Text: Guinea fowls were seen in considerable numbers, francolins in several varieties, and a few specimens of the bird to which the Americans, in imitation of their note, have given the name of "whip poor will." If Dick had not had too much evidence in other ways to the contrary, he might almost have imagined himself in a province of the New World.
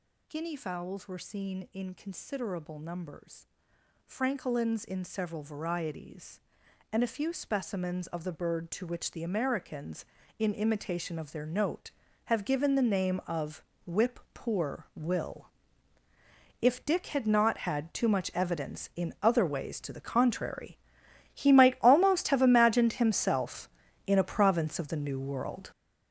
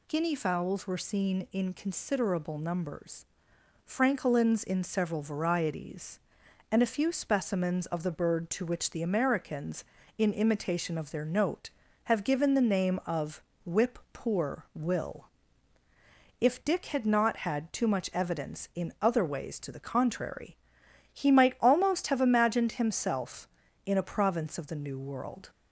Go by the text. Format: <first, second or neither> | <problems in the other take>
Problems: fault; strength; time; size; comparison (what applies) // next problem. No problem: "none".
second | gets louder; strong; throughout; 10 dB // pauses between "of" and "whip"; slight; at 13.6 s; 0.24 s long; slight in the second // pauses between "whip" and "poor"; slight; at 14.1 s; 0.16 s long; slight in the second